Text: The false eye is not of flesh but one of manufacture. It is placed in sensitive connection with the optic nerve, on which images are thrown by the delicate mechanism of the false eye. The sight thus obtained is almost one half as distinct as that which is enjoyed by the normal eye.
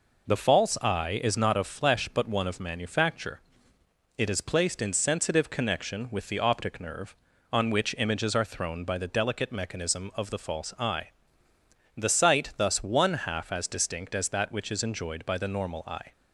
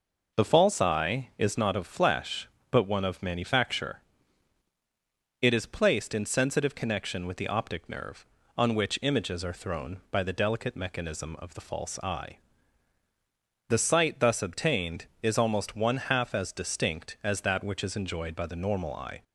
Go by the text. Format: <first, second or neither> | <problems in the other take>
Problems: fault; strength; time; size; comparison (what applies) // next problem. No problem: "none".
second | skips "obtained is almost"; at 12.8 s